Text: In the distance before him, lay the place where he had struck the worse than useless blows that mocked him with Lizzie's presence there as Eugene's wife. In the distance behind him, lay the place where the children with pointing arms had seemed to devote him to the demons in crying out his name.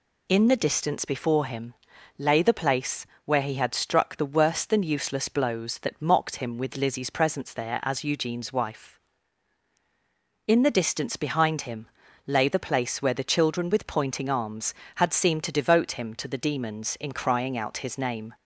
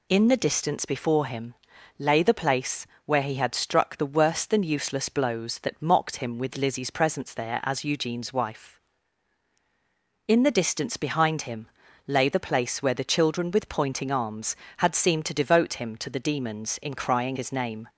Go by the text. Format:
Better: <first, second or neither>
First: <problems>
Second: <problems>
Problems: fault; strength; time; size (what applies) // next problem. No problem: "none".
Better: first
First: pauses between "place" and "where"; slight; at 3.0 s; 0.20 s long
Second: pauses between "place" and "where"; slight; at 2.8 s; 0.20 s long // skips "out"; at 17.3 s